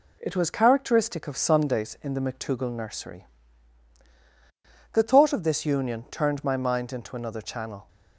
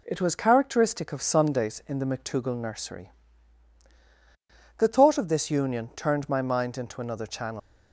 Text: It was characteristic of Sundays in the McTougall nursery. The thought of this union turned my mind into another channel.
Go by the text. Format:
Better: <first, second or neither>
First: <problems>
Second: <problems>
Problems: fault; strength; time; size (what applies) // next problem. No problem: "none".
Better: first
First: none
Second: leaves "channel" unfinished; at 7.5 s; 125 ms